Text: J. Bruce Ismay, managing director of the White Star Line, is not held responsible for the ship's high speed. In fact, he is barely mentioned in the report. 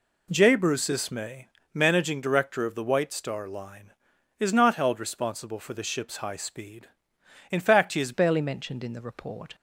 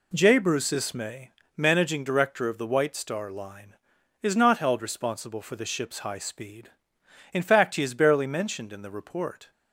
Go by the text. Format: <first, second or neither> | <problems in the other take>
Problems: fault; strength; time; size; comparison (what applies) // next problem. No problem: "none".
second | changes voice at "barely"; from 8.1 s on; 1.4 s long